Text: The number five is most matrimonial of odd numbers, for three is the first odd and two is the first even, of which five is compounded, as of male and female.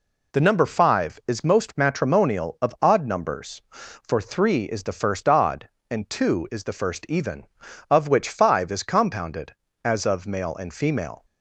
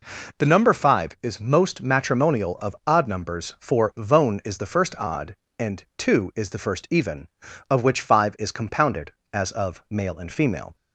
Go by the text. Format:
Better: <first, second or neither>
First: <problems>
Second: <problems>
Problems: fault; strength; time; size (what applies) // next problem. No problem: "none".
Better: first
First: none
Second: says "vone" for "three"; at 3.9 s